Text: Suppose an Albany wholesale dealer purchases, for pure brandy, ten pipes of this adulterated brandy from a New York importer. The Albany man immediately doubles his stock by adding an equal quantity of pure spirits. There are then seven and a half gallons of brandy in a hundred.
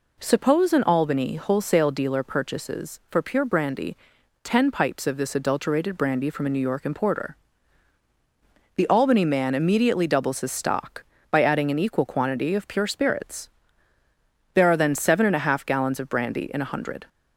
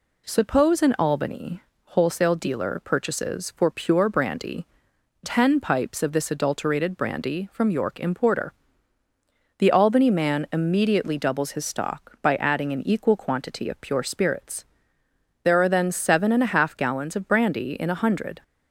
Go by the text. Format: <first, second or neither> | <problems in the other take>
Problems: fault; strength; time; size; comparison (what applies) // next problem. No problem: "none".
first | pauses between "Albany" and "wholesale"; slight; at 1.6 s; 0.22 s long // skips "a New"; at 7.6 s